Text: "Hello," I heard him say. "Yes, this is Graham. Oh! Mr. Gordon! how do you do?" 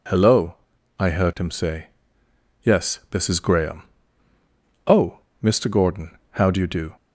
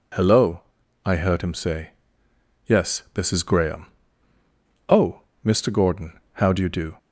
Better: neither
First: none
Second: none

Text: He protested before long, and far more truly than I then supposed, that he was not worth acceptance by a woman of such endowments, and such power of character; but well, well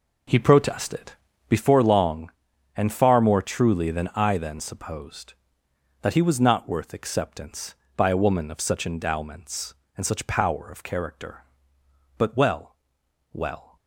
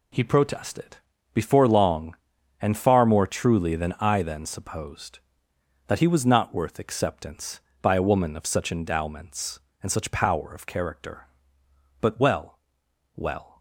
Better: second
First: starts louder than the rest; noticeable; until 1.7 s; 4 dB // pauses between "protested" and "before"; slight; at 1.1 s; 0.36 s long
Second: pauses between "protested" and "before"; slight; at 0.9 s; 0.36 s long

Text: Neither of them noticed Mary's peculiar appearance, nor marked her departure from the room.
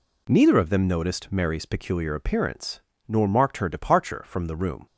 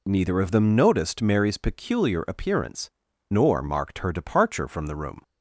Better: neither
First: none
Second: none

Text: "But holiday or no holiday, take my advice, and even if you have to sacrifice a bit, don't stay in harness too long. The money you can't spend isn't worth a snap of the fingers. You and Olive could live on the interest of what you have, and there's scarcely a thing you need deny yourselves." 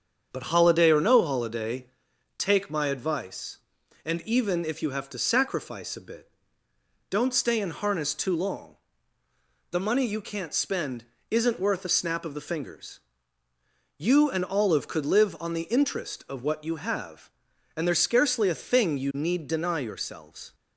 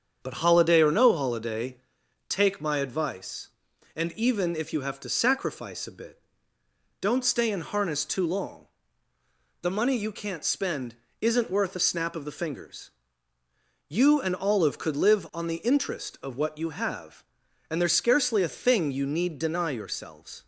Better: neither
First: starts louder than the rest; strong; until 1.3 s; 7.5 dB // pauses between "spend" and "isn't"; slight; at 11.0 s; 0.26 s long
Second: starts louder than the rest; strong; until 1.2 s; 7.5 dB // pauses between "spend" and "isn't"; slight; at 10.9 s; 0.26 s long

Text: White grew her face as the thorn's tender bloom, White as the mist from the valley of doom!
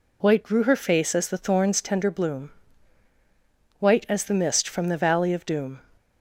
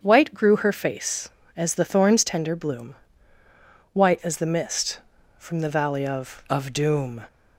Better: first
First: none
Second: starts louder than the rest; until 1.0 s; 7 dB // says "of" twice; at 6.4 s

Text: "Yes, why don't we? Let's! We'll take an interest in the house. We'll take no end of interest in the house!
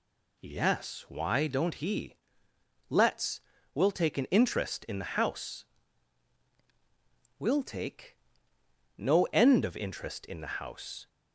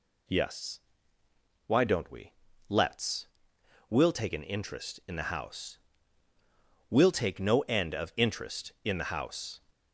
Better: second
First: says "he" for "we"; at 1.7 s // pauses between "take" and "no"; noticeable; at 8.1 s; 0.80 s long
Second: none

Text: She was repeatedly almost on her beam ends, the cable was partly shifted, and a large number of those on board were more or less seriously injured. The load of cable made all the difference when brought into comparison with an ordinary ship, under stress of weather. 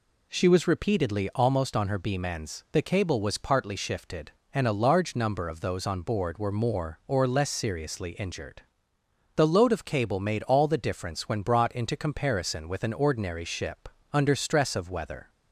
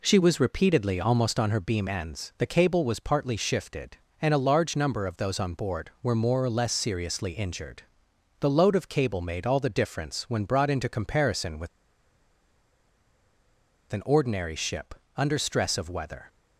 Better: first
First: none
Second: pauses between "with" and "an"; strong; at 11.6 s; 2.2 s long

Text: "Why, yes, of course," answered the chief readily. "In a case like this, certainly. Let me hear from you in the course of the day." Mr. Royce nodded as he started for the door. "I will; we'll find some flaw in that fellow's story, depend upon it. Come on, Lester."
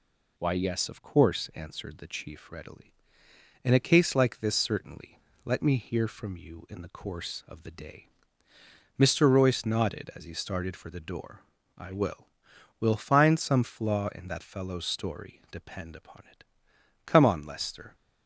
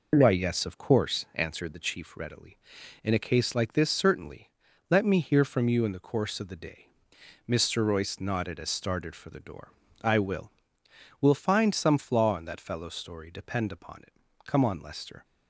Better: first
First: none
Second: skips "he"; at 8.6 s

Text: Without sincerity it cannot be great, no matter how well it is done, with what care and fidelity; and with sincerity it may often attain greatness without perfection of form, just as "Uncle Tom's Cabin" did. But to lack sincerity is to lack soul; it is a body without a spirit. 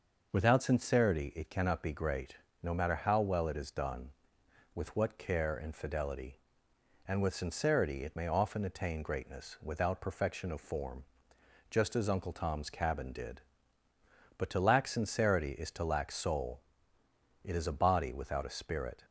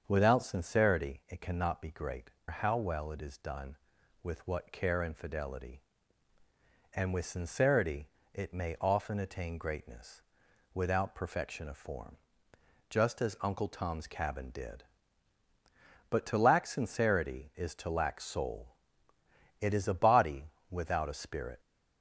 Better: first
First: none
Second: starts louder than the rest; until 1.0 s; 7 dB // skips "no matter"; at 2.3 s // pauses between "sincerity" and "it"; slight; at 8.0 s; 0.28 s long // pauses between "greatness" and "without"; noticeable; at 10.1 s; 0.54 s long // pauses between "body" and "without"; slight; at 20.4 s; 0.20 s long

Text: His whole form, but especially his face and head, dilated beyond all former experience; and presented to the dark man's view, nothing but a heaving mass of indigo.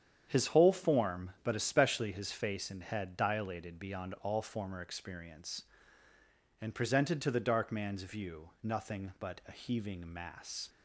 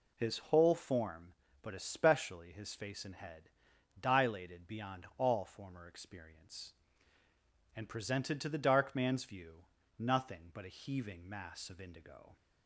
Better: second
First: starts louder than the rest; strong; until 1.2 s; 8.5 dB // stops before "of indigo"; at 10.6 s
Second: none

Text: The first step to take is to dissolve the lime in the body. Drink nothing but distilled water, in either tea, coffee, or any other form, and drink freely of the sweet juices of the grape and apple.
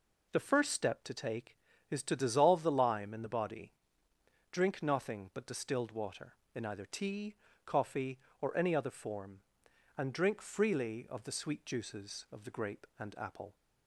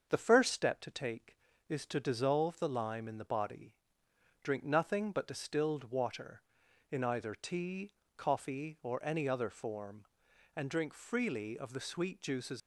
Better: first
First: none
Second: starts louder than the rest; until 1.1 s; 7 dB // stops before "of the grape and apple"; at 12.6 s

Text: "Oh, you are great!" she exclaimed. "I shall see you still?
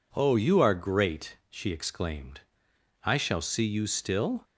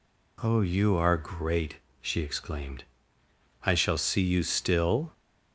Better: neither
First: none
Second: none

